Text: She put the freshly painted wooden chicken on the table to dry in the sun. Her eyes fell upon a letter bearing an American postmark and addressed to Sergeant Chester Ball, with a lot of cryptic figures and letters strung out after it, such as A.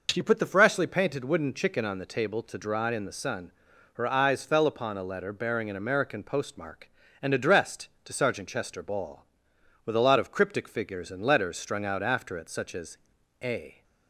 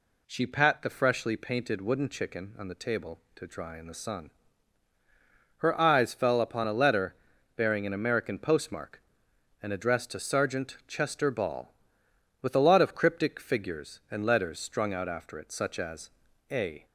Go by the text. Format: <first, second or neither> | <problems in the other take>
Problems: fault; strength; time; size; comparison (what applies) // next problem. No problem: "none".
first | says "pat" for "put"; at 0.4 s // pauses between "letter" and "bearing"; at 7.1 s; 0.40 s long // pauses between "as" and "A"; at 16.0 s; 0.42 s long; noticeable in the first